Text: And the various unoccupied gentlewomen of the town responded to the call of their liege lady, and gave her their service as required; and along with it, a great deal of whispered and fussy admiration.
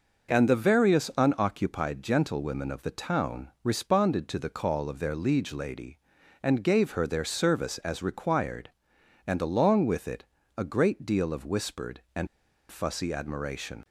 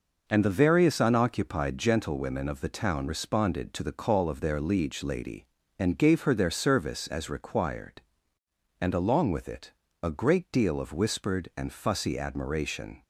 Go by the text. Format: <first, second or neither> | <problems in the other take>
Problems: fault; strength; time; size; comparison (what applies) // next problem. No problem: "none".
second | pauses between "town" and "responded"; slight; at 3.4 s; 0.16 s long // pauses between "and" and "fussy"; at 12.2 s; 0.43 s long